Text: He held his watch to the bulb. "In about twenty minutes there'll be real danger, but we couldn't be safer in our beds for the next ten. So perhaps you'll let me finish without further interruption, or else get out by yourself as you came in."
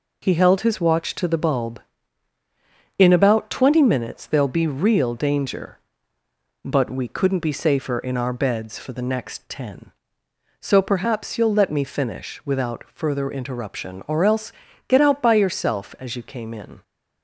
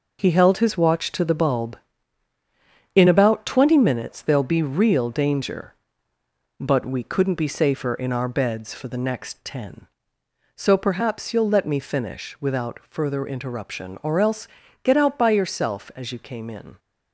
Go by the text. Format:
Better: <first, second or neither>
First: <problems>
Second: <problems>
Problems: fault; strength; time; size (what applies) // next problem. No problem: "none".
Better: first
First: pauses between "else" and "get"; slight; at 14.5 s; 0.34 s long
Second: gets quieter; strong; throughout; 7.5 dB // pauses between "else" and "get"; slight; at 14.4 s; 0.34 s long